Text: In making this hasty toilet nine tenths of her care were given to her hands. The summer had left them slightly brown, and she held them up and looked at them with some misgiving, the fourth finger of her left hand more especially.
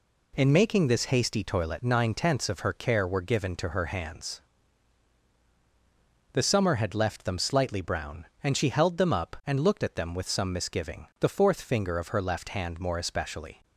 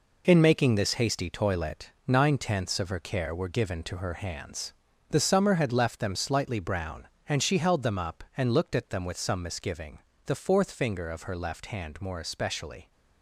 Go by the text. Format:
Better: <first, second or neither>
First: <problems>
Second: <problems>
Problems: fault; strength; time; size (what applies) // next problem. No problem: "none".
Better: first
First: none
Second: gets quieter; strong; throughout; 7.5 dB // pauses between "toilet" and "nine"; slight; at 1.9 s; 0.16 s long